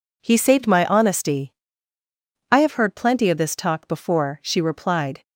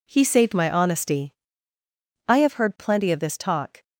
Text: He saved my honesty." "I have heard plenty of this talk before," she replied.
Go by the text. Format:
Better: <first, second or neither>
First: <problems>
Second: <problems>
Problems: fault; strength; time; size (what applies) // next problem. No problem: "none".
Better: first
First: none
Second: stops before "before she replied"; at 3.8 s